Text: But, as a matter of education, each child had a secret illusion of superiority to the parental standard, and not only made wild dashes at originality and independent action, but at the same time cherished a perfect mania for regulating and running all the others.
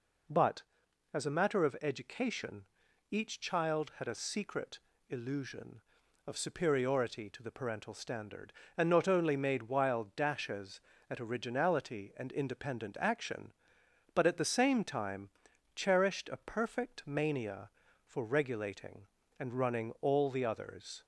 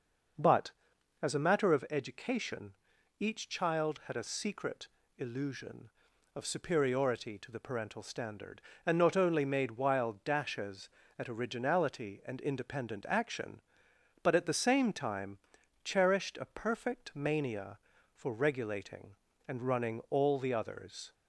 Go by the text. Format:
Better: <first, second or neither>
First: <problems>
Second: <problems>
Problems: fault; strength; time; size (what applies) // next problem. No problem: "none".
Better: first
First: pauses between "secret" and "illusion"; slight; at 4.7 s; 0.30 s long // pauses between "time" and "cherished"; noticeable; at 15.2 s; 0.46 s long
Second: starts louder than the rest; noticeable; until 1.9 s; 6 dB // pauses between "secret" and "illusion"; slight; at 4.8 s; 0.30 s long // pauses between "time" and "cherished"; noticeable; at 15.3 s; 0.46 s long